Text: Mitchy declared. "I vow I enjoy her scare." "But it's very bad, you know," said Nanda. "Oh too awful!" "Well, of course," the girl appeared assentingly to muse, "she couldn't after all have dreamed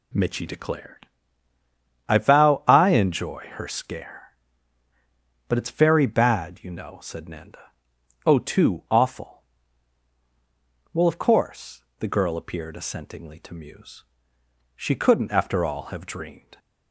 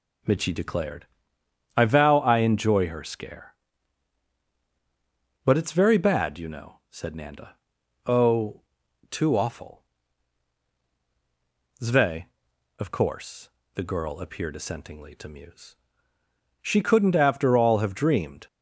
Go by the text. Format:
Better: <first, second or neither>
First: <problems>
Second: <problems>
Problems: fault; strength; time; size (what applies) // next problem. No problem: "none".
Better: first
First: none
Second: pauses between "Oh" and "too"; noticeable; at 8.6 s; 0.48 s long // says "Zve" for "Well"; at 11.8 s